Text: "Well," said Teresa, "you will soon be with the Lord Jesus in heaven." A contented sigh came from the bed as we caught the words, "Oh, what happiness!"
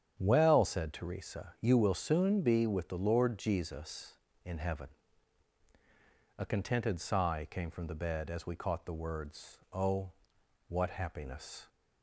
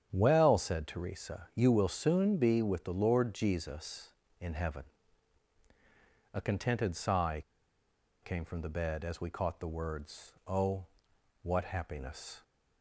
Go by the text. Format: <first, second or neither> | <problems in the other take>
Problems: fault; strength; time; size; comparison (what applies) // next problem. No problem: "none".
first | starts louder than the rest; strong; until 1.1 s; 9 dB; strong in the first // pauses between "sigh" and "came"; noticeable; at 7.4 s; 0.80 s long